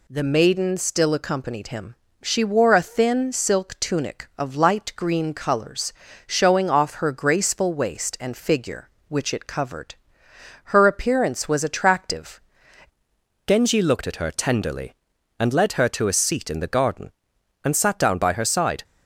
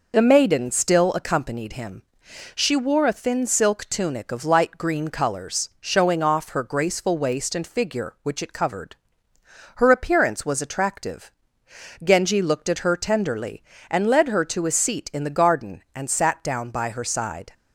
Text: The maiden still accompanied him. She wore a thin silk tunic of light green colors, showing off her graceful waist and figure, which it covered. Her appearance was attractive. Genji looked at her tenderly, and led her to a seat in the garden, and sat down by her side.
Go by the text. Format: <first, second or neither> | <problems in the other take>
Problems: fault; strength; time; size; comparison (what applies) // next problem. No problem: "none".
second | changes voice at "Genji"; from 13.4 s on; 5.4 s long